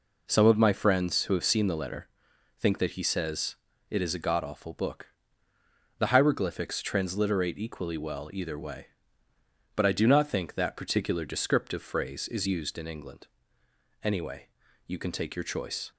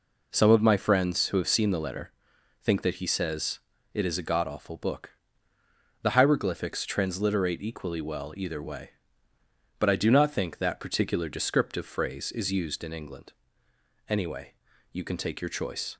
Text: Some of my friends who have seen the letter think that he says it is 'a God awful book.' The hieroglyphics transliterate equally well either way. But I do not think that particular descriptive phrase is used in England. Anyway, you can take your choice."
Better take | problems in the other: neither | pauses between "letter" and "think"; noticeable; the same in both // pauses between "says" and "it"; slight; the same in both

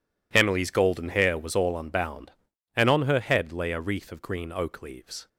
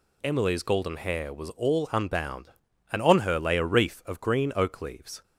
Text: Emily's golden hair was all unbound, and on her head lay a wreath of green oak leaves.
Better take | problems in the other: first | skips "head"; at 3.3 s

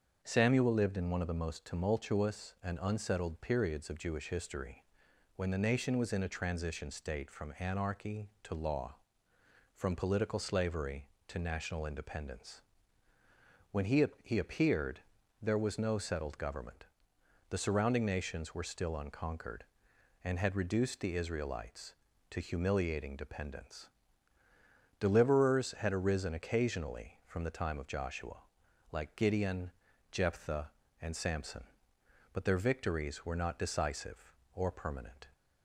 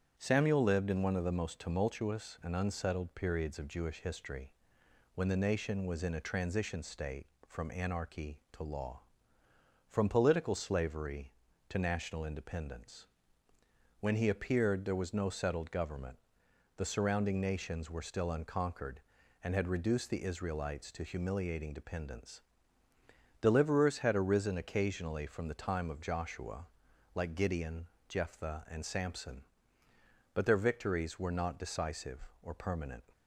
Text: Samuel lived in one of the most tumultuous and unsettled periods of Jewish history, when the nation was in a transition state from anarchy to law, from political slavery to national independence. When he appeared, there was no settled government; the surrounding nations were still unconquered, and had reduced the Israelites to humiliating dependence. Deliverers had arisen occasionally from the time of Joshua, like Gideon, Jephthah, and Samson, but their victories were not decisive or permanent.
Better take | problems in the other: second | starts louder than the rest; until 1.2 s; 7 dB; strong in the second // says "he" twice; at 14.2 s

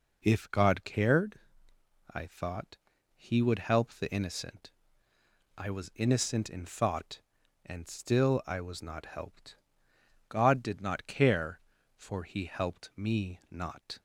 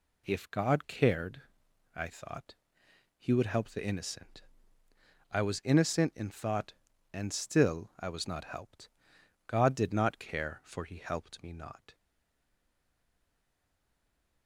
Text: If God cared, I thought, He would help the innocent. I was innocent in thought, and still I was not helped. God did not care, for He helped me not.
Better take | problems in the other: first | stays silent after the last word; from 11.9 s on; 2.5 s long

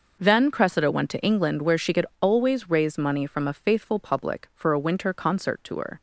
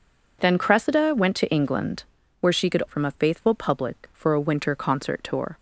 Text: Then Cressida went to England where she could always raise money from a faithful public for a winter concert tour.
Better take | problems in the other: first | pauses between "England" and "where"; slight; at 2.0 s; 0.36 s long // skips "always raise money"; at 2.8 s

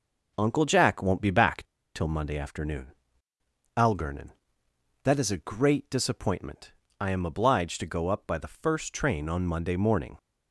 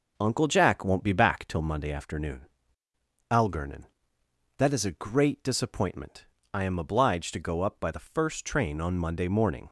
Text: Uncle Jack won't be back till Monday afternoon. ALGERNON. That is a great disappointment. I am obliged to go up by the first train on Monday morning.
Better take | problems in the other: second | pauses between "back" and "till"; slight; at 1.6 s; 0.31 s long

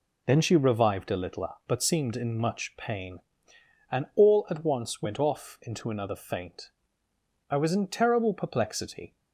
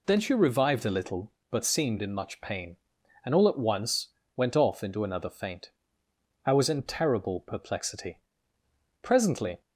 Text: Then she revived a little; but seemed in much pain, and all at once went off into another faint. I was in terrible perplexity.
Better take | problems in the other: first | pauses between "once" and "went"; slight; at 4.0 s; 0.28 s long // goes on to say "Presently"; from 9.0 s on; 0.60 s long

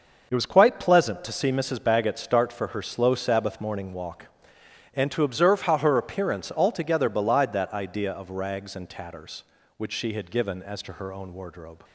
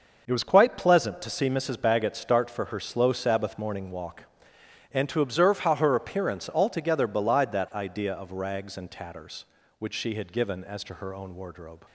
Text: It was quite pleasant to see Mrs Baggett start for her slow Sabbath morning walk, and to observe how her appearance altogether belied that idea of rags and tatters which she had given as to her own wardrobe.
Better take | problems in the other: neither | none

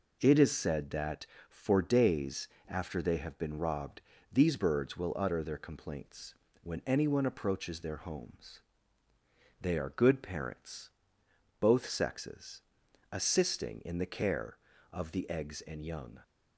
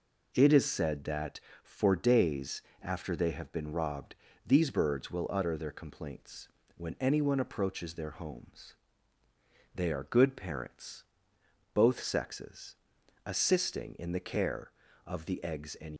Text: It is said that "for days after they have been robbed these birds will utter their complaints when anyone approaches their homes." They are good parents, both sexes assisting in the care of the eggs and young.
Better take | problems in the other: first | pauses between "days" and "after"; slight; at 2.6 s; 0.18 s long; slight in the first // pauses between "robbed" and "these"; slight; at 4.1 s; 0.32 s long; slight in the first // pauses between "complaints" and "when"; slight; at 6.4 s; 0.28 s long; slight in the first // pauses between "sexes" and "assisting"; noticeable; at 12.7 s; 0.50 s long; noticeable in the first // stops before "young"; at 15.9 s

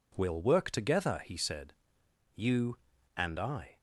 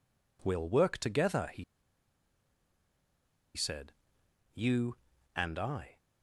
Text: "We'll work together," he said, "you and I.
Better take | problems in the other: first | pauses between "he" and "said"; strong; at 1.6 s; 1.9 s long

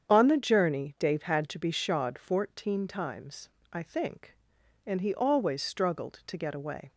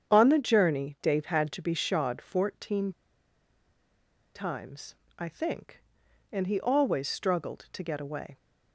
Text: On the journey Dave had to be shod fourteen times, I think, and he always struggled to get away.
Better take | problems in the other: first | starts louder than the rest; strong; until 1.1 s; 8 dB; strong in the first // pauses between "fourteen" and "times"; strong; at 2.9 s; 1.4 s long

